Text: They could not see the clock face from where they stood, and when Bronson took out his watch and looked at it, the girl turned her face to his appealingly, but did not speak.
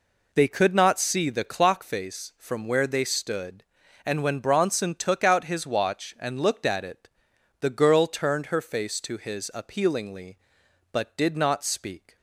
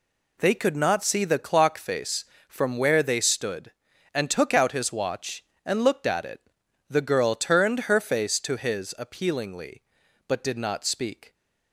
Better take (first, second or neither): first